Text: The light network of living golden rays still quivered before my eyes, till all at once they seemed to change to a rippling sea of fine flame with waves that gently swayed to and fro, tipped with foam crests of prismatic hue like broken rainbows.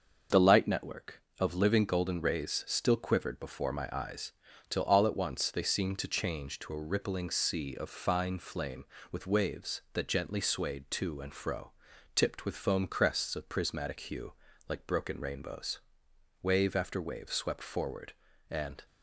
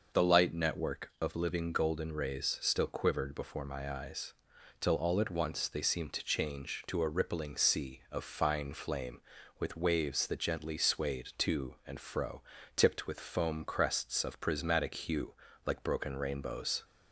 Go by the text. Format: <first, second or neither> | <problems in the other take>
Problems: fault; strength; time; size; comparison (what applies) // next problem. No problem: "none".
second | starts louder than the rest; until 1.5 s; 6.5 dB // pauses between "hue" and "like"; at 14.3 s; 0.38 s long; slight in the second // goes on to say "Wave after wave swept forward and"; strong; from 16.4 s on; 2.4 s long